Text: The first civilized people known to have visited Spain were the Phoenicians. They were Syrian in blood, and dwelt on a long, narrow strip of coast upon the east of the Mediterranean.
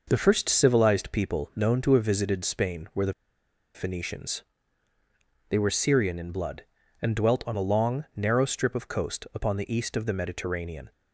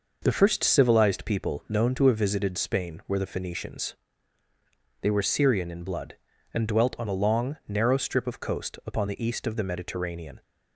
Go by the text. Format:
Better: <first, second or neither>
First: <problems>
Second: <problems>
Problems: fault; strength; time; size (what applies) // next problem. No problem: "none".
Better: second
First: pauses between "the" and "Phoenicians"; noticeable; at 3.1 s; 0.62 s long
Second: none